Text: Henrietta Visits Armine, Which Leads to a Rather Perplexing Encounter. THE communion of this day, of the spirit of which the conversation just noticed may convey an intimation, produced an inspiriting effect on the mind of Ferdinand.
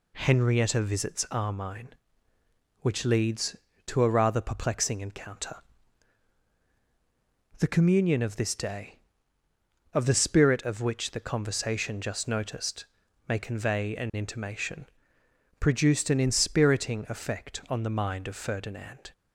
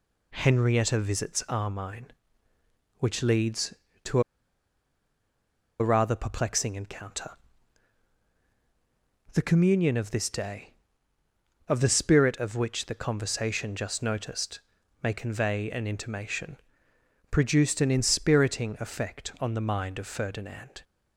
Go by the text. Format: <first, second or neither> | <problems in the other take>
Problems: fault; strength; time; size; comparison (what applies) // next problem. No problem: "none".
first | pauses between "to" and "a"; strong; at 4.2 s; 1.5 s long // pauses between "noticed" and "may"; at 14.5 s; 0.44 s long; also in the first